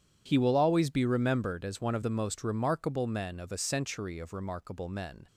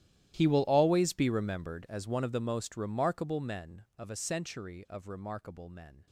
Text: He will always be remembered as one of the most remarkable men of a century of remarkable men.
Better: first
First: none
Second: gets quieter; strong; throughout; 21.5 dB

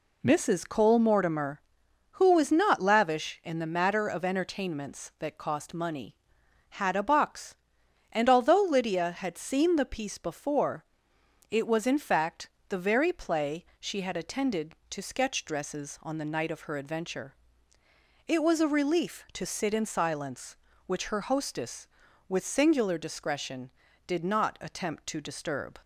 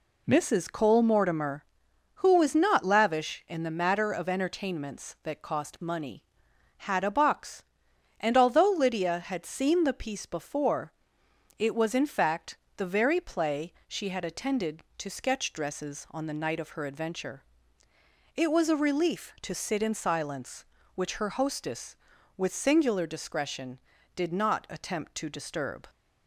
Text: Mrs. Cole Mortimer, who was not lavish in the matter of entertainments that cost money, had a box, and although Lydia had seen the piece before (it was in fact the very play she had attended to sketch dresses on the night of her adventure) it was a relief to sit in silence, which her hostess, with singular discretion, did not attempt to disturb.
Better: neither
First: pauses between "fact" and "the"; slight; at 12.4 s; 0.18 s long // pauses between "play" and "she"; slight; at 13.6 s; 0.16 s long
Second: pauses between "fact" and "the"; slight; at 12.5 s; 0.18 s long // pauses between "play" and "she"; slight; at 13.7 s; 0.16 s long

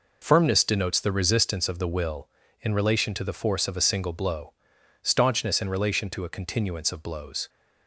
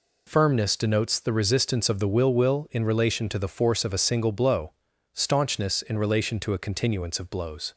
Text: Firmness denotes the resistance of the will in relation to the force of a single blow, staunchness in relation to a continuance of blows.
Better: first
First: none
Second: says "will" twice; at 2.3 s

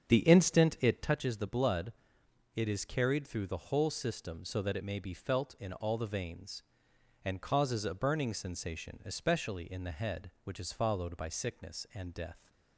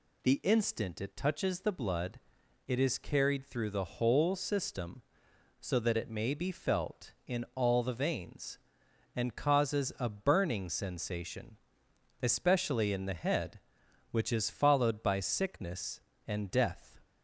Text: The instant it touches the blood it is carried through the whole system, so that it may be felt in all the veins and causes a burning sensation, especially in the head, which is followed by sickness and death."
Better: second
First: starts louder than the rest; strong; until 1.2 s; 7.5 dB // pauses between "blood" and "it"; noticeable; at 1.9 s; 0.62 s long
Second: pauses between "blood" and "it"; noticeable; at 2.1 s; 0.48 s long

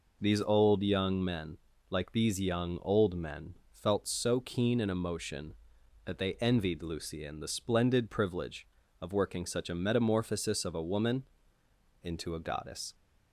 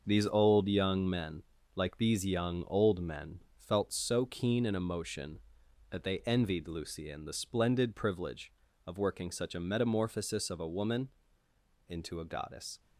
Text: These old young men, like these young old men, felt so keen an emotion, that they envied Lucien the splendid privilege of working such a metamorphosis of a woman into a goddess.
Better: first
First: pauses between "woman" and "into"; noticeable; at 11.2 s; 0.78 s long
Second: gets quieter; strong; throughout; 7.5 dB // pauses between "woman" and "into"; noticeable; at 11.0 s; 0.78 s long

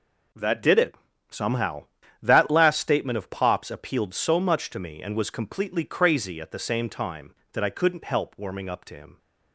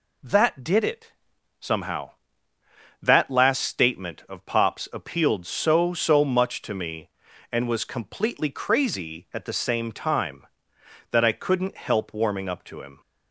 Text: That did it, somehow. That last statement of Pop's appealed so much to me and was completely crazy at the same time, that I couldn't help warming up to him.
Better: first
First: none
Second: says "so" twice; at 5.9 s

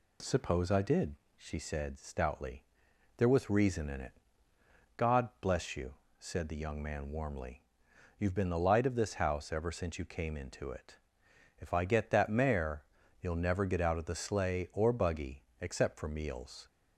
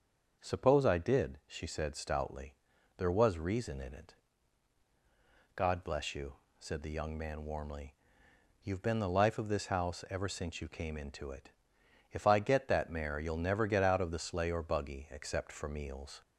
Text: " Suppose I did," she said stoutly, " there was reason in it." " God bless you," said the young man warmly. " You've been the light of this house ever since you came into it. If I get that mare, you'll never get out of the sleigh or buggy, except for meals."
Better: first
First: none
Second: starts louder than the rest; until 1.5 s; 6.5 dB // says "life" for "light"; at 9.0 s

